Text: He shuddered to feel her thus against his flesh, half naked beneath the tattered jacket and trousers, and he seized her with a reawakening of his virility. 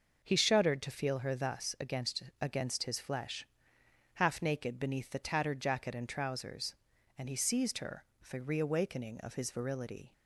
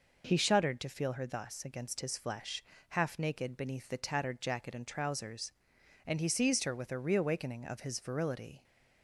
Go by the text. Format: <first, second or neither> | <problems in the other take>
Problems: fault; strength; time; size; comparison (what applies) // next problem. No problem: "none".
second | says "against" twice; at 2.4 s